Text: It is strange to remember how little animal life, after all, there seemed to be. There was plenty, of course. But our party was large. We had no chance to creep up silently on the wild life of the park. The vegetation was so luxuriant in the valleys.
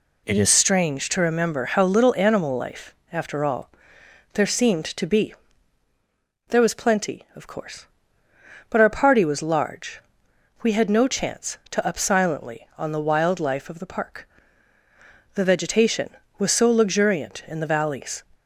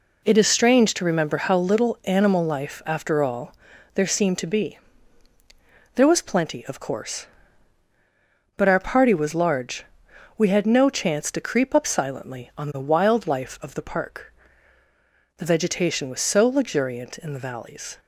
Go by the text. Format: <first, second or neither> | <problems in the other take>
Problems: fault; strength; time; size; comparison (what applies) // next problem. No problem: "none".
second | skips "creep"; at 11.8 s